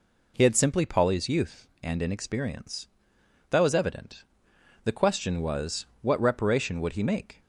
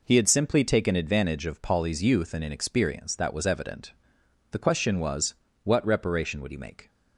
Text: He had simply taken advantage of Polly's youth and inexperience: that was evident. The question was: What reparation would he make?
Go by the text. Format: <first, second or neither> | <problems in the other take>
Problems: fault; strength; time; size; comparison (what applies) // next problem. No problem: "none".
second | skips "taken advantage of"; at 0.8 s